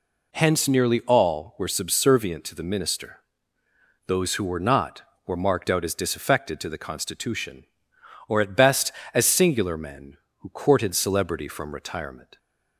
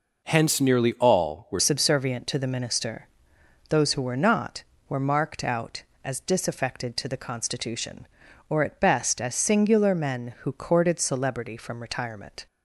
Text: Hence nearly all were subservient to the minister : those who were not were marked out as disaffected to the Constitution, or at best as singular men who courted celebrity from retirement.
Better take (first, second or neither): first